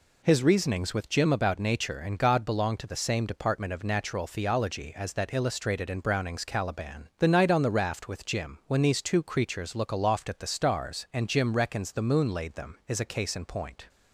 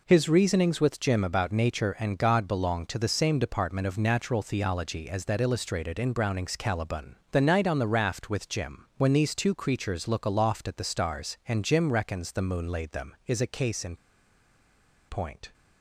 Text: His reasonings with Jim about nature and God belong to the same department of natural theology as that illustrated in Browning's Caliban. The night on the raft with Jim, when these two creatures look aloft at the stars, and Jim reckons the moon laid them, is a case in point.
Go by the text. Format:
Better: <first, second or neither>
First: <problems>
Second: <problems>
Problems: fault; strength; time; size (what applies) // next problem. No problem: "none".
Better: first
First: none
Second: pauses between "in" and "point"; at 13.9 s; 1.1 s long